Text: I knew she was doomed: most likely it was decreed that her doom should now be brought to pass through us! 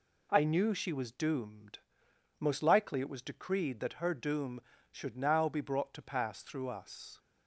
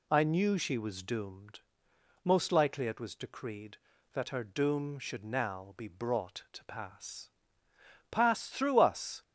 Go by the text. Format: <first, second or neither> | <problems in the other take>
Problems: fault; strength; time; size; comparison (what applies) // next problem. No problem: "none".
first | says "pass" twice; at 8.0 s